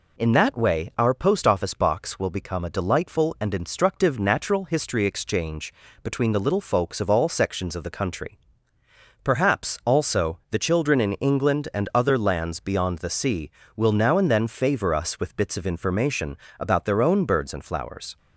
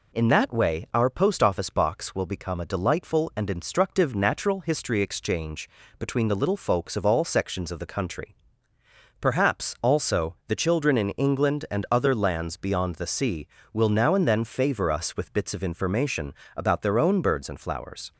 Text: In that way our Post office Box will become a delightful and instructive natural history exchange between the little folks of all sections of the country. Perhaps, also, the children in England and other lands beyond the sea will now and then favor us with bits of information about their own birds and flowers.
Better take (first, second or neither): neither